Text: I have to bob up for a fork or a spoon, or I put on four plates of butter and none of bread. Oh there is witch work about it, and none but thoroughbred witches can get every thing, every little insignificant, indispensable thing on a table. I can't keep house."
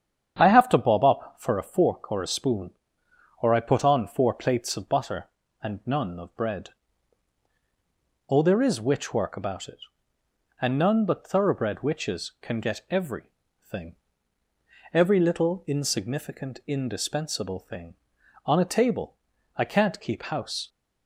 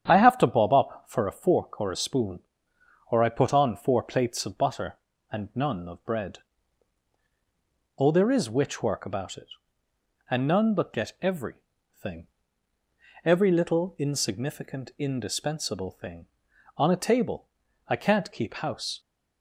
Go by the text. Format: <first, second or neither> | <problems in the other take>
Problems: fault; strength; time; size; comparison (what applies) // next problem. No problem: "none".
first | starts louder than the rest; strong; until 1.1 s; 9 dB; strong in the first // skips "thoroughbred witches can"; at 10.9 s // pauses between "every" and "thing"; noticeable; at 11.5 s; 0.48 s long; noticeable in the first